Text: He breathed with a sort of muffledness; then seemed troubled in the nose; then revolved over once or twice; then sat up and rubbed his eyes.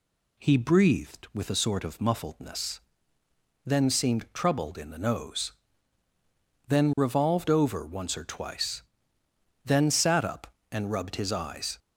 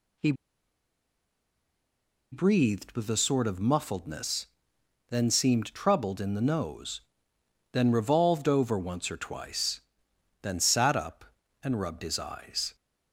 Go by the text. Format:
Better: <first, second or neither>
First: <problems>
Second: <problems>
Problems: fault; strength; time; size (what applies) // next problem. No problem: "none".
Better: first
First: none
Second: pauses between "He" and "breathed"; strong; at 0.3 s; 1.9 s long